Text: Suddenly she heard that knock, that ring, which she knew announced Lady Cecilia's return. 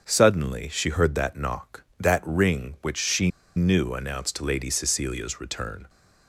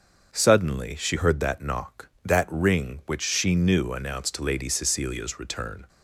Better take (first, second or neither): second